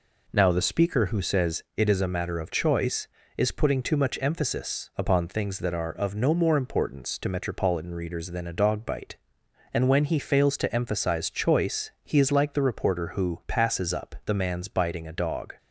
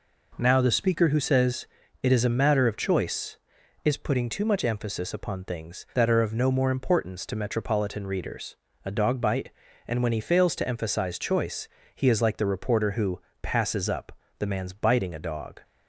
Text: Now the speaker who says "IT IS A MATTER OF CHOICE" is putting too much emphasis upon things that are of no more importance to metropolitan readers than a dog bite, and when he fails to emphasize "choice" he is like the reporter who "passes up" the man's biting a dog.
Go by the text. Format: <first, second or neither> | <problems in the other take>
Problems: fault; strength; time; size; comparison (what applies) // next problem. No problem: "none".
first | pauses between "says" and "IT"; slight; at 1.6 s; 0.34 s long // skips "than"; at 8.6 s // pauses between "choice" and "he"; slight; at 11.6 s; 0.26 s long // pauses between "who" and "passes"; slight; at 13.2 s; 0.22 s long // pauses between "up" and "the"; slight; at 14.1 s; 0.28 s long